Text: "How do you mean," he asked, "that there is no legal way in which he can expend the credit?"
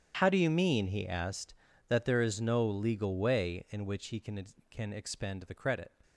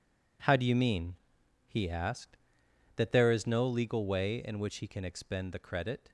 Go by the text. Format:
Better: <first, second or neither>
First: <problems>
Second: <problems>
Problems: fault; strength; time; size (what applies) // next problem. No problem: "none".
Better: second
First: starts louder than the rest; strong; until 1.2 s; 9 dB // says "can" twice; at 4.6 s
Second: none